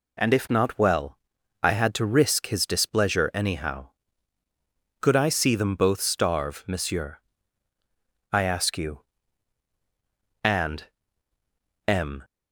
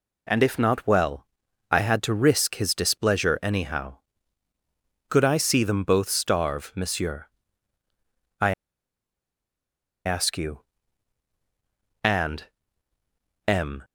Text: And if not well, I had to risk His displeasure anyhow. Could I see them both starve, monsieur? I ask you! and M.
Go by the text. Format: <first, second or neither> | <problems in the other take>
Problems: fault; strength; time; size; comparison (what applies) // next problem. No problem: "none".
first | pauses between "I" and "ask"; strong; at 8.5 s; 1.5 s long // pauses between "and" and "M"; at 12.4 s; 1.0 s long; also in the first